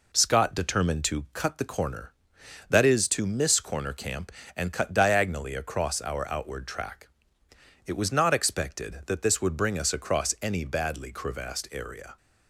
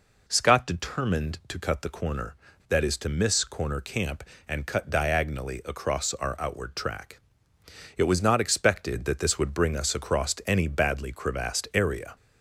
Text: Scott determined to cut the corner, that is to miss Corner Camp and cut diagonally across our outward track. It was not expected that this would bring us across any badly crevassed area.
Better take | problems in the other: neither | none

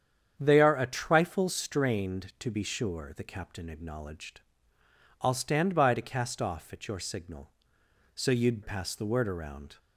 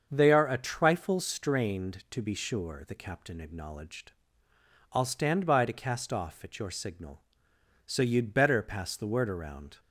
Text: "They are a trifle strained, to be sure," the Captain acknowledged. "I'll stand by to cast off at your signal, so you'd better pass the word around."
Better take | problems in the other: second | starts louder than the rest; strong; until 1.3 s; 8.5 dB; also in the second // skips "better"; at 8.6 s

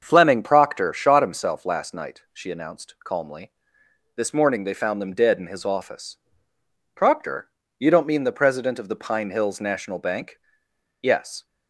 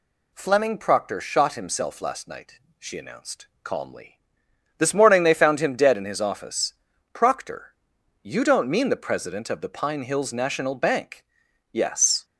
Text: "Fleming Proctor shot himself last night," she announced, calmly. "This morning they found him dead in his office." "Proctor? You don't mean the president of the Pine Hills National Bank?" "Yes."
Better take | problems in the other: second | starts louder than the rest; until 1.0 s; 6.5 dB // says "them" for "him"; at 5.0 s

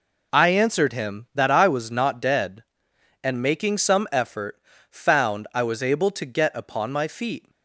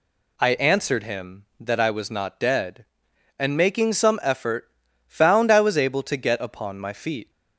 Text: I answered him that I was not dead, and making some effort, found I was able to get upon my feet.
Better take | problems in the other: neither | none

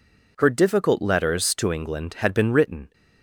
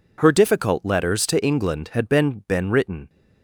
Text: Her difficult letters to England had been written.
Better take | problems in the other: first | says "been" twice; at 2.4 s

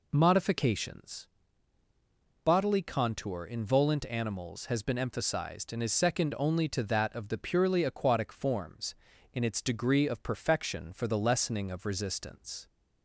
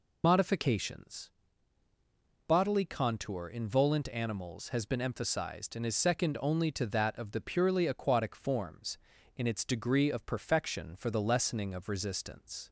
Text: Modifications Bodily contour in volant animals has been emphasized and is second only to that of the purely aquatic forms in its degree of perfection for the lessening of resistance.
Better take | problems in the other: first | loses the start of "Modifications"; at 0.2 s; 90 ms // pauses between "Modifications" and "Bodily"; at 1.3 s; 1.1 s long; also in the first

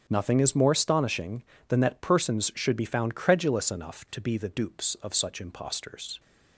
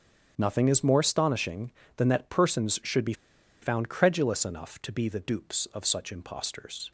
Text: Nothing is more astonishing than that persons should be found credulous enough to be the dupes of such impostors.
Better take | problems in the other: first | starts louder than the rest; strong; until 1.3 s; 8 dB; strong in the first // pauses between "be" and "found"; noticeable; at 3.1 s; 0.48 s long

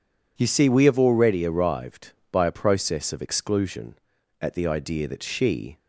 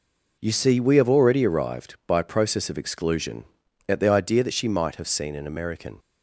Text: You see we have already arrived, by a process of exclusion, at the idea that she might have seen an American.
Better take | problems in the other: second | stops before "might have seen an American"; at 5.7 s

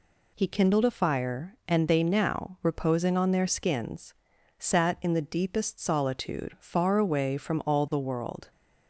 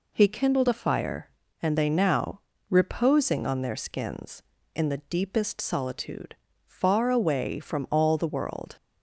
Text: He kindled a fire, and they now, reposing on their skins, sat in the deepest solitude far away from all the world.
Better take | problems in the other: first | skips "sat"; at 4.5 s // pauses between "solitude" and "far"; slight; at 6.3 s; 0.32 s long

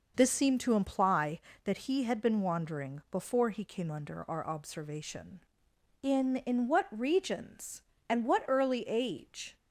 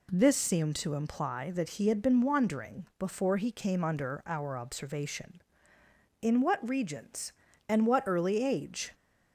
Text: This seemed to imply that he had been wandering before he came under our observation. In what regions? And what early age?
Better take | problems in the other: second | says "In" twice; at 6.3 s

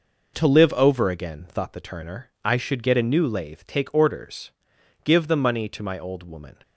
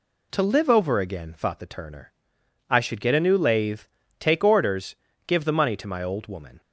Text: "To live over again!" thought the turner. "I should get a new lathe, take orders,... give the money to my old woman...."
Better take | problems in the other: neither | none

